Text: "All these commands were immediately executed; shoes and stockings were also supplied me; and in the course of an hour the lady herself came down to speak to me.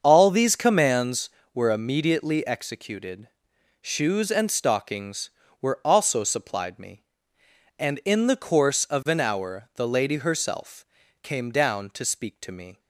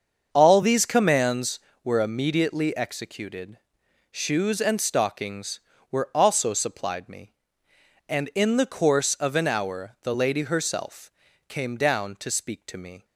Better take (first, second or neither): neither